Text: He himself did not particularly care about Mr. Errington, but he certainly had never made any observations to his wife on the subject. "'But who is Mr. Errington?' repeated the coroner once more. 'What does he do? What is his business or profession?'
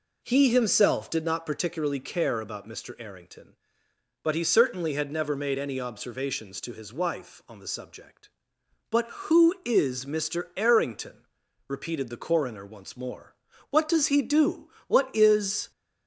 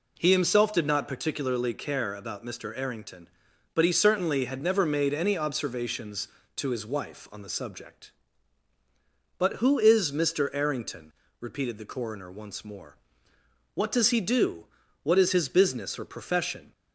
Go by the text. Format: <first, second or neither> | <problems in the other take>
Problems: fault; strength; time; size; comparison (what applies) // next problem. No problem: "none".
second | stops before "his business or profession"; at 15.7 s